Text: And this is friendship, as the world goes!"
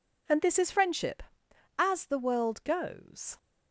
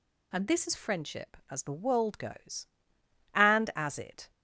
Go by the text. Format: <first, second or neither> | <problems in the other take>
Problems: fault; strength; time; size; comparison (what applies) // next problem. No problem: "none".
first | goes on to say "And as it"; noticeable; from 3.3 s on; 0.96 s long